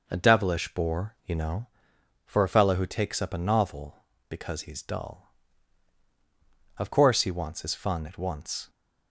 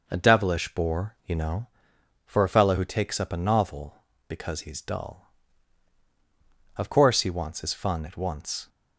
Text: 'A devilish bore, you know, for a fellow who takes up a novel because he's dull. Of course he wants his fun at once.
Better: neither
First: none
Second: none

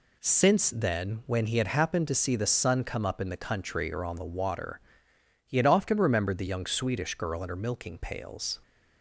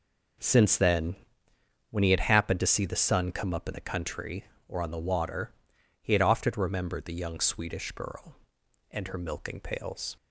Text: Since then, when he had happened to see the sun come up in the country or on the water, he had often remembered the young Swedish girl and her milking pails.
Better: neither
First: none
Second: none

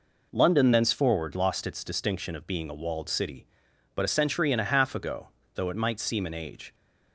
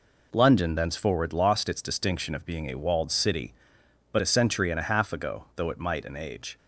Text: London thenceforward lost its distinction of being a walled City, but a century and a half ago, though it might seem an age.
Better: first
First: none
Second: skips "seem"; at 6.0 s

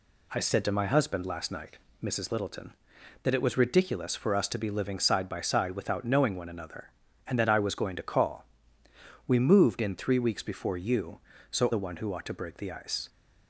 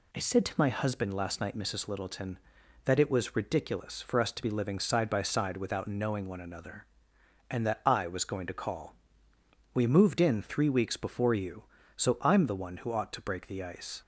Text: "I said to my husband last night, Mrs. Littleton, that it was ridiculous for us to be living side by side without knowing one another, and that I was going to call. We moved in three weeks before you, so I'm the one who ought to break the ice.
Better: second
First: skips "I'm"; at 11.7 s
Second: none

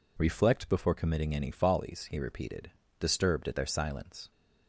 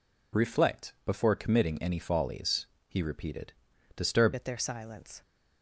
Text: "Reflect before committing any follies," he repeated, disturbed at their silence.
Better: first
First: none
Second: changes voice at "at"; from 4.3 s on; 0.9 s long

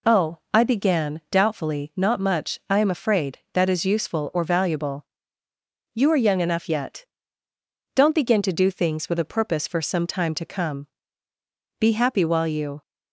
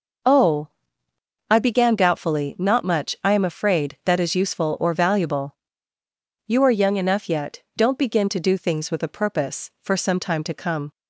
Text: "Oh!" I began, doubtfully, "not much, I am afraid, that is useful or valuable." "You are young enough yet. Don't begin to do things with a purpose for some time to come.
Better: second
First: goes on to say "Be happy while you"; noticeable; from 11.7 s on; 1.0 s long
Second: none

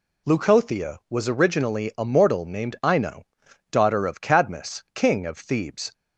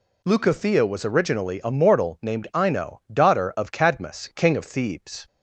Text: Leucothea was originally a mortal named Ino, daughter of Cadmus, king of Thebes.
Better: neither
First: none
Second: none

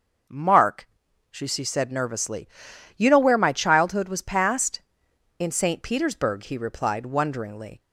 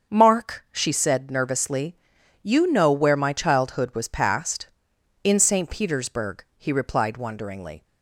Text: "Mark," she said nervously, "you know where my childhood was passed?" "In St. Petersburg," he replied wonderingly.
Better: second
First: starts louder than the rest; noticeable; until 1.7 s; 6 dB // says "she" twice; at 1.4 s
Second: starts louder than the rest; until 1.1 s; 6.5 dB

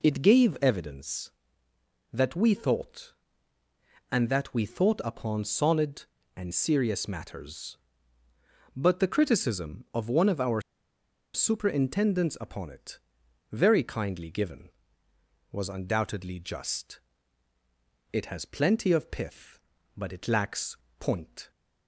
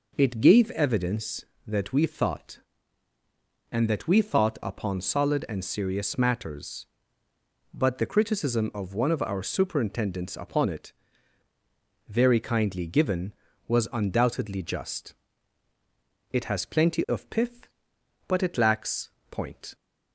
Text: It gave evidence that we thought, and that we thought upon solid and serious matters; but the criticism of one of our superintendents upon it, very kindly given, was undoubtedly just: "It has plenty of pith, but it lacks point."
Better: second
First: pauses between "our" and "superintendents"; noticeable; at 10.5 s; 0.74 s long // pauses between "lacks" and "point"; slight; at 20.7 s; 0.22 s long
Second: pauses between "lacks" and "point"; slight; at 19.1 s; 0.18 s long

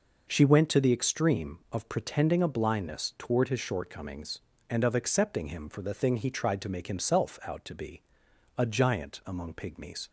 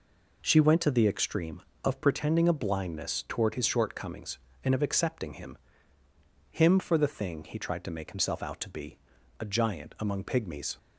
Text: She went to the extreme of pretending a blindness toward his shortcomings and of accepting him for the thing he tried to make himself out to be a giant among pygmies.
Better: first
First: pauses between "be" and "a"; noticeable; at 8.0 s; 0.52 s long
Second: says "him" twice; at 6.5 s // pauses between "be" and "a"; at 8.9 s; 0.42 s long

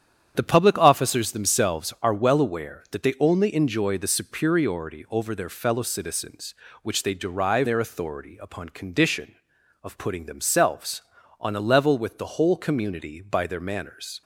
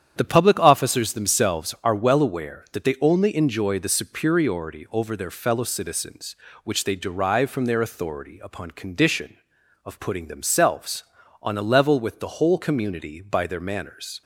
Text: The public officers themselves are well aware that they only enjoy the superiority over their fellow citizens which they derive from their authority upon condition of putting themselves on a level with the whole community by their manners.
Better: second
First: starts louder than the rest; strong; until 1.3 s; 9 dB // skips "from"; at 7.6 s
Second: starts louder than the rest; strong; until 1.1 s; 9 dB

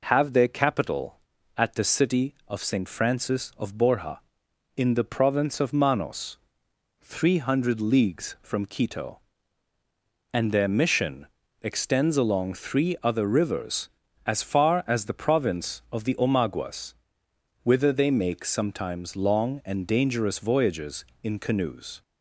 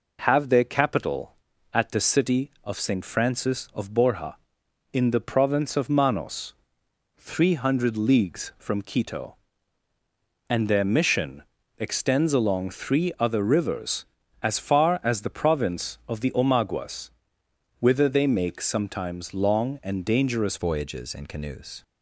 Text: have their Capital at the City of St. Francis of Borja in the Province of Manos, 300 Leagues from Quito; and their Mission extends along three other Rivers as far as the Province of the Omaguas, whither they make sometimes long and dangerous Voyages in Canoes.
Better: first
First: pauses between "Mission" and "extends"; slight; at 11.2 s; 0.36 s long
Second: pauses between "Mission" and "extends"; slight; at 11.4 s; 0.36 s long // changes voice at "Voyages"; from 20.5 s on; 1.3 s long

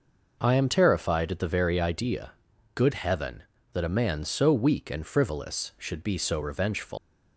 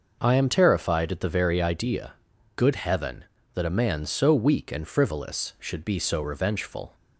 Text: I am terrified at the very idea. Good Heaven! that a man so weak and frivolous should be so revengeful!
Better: second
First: leaves "revengeful" unfinished; at 6.9 s; 145 ms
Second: none

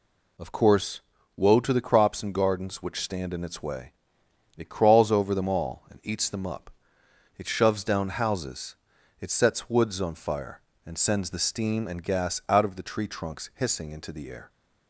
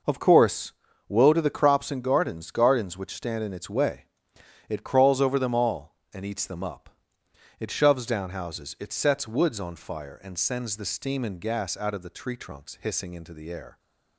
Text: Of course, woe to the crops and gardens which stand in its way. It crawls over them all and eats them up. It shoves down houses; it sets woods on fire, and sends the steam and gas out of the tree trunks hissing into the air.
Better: first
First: none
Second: says "gardens" twice; at 2.5 s

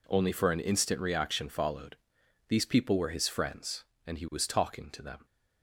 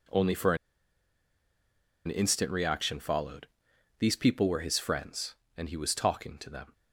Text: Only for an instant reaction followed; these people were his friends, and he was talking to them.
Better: first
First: none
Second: pauses between "for" and "an"; strong; at 0.5 s; 1.5 s long

